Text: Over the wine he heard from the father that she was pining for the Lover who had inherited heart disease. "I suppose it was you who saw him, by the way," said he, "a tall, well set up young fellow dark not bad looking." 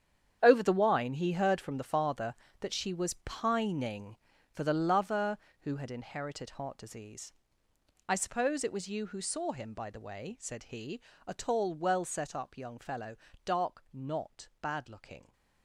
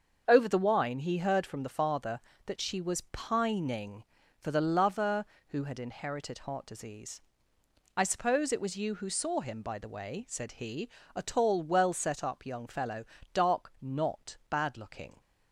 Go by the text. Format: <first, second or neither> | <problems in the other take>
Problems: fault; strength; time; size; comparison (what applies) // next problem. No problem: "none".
second | gets quieter; strong; throughout; 13.5 dB // starts louder than the rest; strong; until 1.4 s; 8.5 dB; also in the second // pauses between "fellow" and "dark"; slight; at 13.1 s; 0.30 s long; slight in the second